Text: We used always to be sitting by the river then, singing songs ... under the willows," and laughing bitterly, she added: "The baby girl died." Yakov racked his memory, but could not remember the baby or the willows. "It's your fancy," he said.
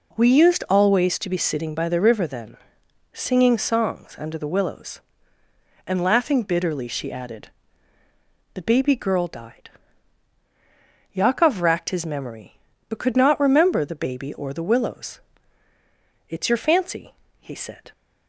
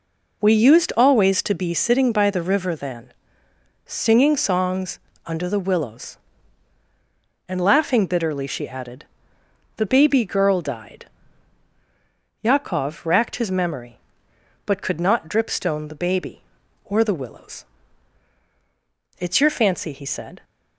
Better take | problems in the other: first | says "dripstone" for "remember"; at 15.2 s

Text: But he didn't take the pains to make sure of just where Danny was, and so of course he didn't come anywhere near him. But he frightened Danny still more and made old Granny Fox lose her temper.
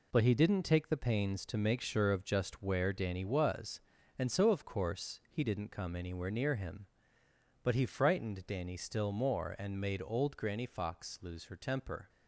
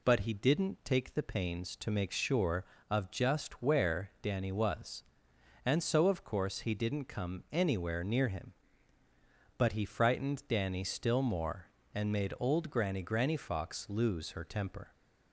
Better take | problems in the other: first | says "Granny" twice; at 13.0 s

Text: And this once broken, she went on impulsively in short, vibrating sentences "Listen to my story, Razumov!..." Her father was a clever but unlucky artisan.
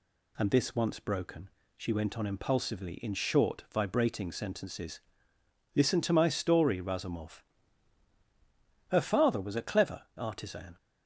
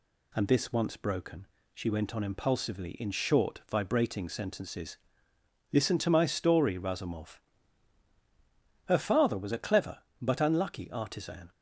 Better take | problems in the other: second | pauses between "sentences" and "Listen"; noticeable; at 5.0 s; 0.74 s long; noticeable in the second // skips "but unlucky"; at 10.0 s

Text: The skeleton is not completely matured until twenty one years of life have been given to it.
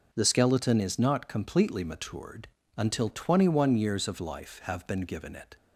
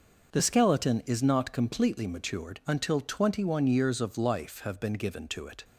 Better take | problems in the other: second | pauses between "matured" and "until"; slight; at 2.4 s; 0.30 s long // skips "to"; at 5.3 s

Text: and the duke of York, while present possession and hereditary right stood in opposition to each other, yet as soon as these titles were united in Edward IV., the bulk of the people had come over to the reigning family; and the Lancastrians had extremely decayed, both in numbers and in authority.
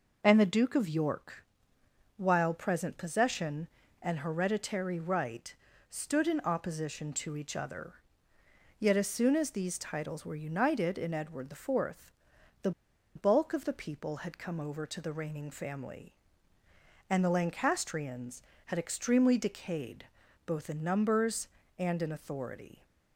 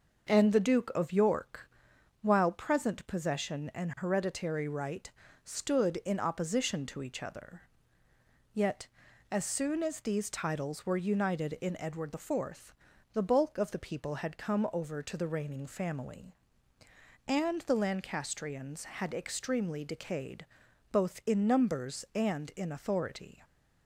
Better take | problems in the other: second | pauses between "right" and "stood"; slight; at 5.5 s; 0.34 s long; slight in the second // pauses between "the" and "bulk"; at 12.7 s; 0.44 s long

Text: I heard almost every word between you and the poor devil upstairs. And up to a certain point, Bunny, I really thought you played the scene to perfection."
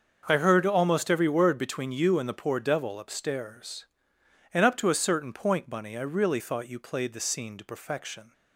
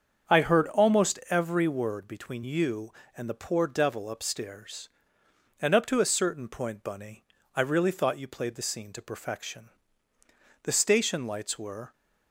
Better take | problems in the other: first | starts louder than the rest; strong; until 1.4 s; 7.5 dB; also in the first // goes on to say "The station lights were"; noticeable; from 10.6 s on; 1.3 s long

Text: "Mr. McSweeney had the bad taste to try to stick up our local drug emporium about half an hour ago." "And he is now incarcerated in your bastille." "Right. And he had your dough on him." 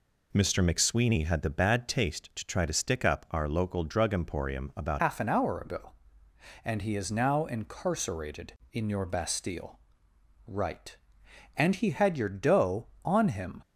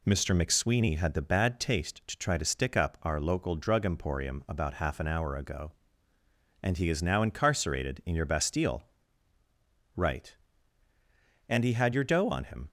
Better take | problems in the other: second | changes voice at "half"; from 4.9 s on; 8.7 s long

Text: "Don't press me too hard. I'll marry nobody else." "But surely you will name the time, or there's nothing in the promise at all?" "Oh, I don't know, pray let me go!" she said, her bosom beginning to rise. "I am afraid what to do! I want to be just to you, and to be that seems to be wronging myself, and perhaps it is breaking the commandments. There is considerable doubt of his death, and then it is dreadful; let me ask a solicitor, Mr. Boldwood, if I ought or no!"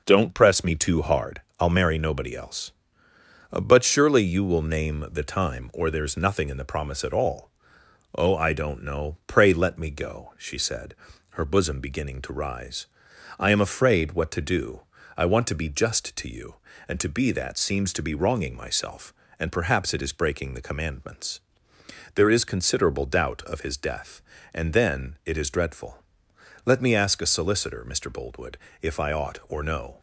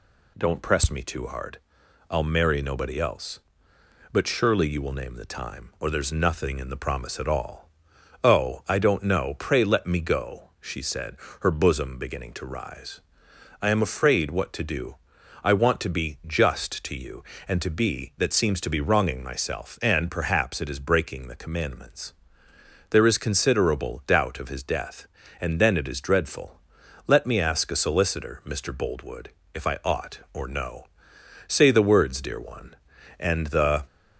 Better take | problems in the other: first | goes on to say "Say the words dear one and the"; strong; from 31.4 s on; 2.3 s long

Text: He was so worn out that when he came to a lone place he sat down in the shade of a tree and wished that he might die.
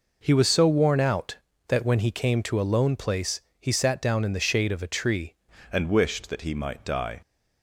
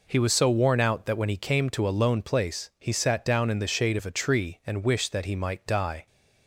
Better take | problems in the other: second | pauses between "place" and "he"; slight; at 3.3 s; 0.20 s long // changes voice at "and"; from 5.7 s on; 1.5 s long

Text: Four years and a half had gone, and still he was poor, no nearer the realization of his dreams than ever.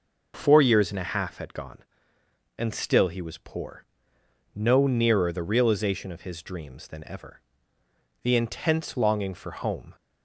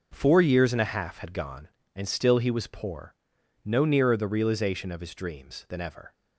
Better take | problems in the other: second | goes on to say "The intense longing for home"; strong; from 8.2 s on; 1.7 s long

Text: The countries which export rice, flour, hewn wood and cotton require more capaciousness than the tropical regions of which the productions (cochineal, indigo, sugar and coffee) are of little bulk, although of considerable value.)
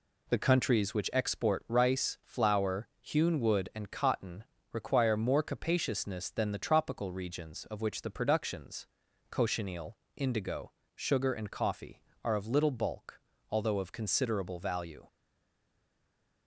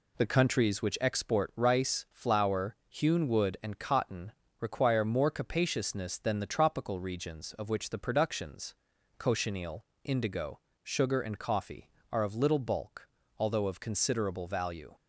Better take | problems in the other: second | pauses between "cotton" and "require"; slight; at 4.4 s; 0.30 s long; slight in the second // stays silent after the last word; noticeable; from 15.0 s on; 1.4 s long

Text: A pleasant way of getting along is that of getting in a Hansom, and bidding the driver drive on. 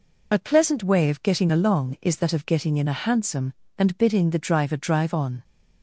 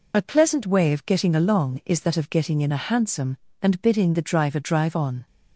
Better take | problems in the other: neither | none

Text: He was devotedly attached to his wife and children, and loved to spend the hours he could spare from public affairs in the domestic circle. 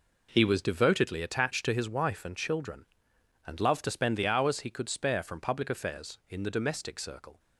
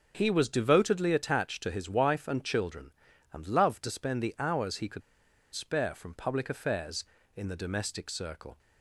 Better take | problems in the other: first | pauses between "could" and "spare"; noticeable; at 5.0 s; 0.52 s long

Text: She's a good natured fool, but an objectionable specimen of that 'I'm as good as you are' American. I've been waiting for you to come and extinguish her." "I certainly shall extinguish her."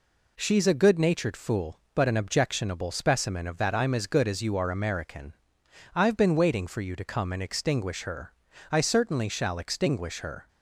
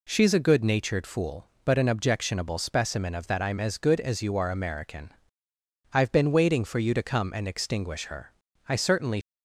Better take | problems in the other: first | stops before "shall extinguish her"; at 9.2 s

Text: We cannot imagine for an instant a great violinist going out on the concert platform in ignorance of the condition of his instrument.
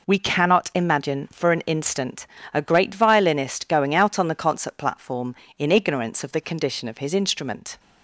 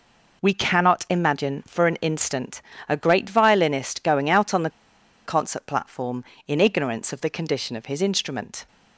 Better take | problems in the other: first | pauses between "instant" and "a"; slight; at 2.6 s; 0.26 s long; slight in the first // pauses between "the" and "concert"; noticeable; at 4.6 s; 0.56 s long

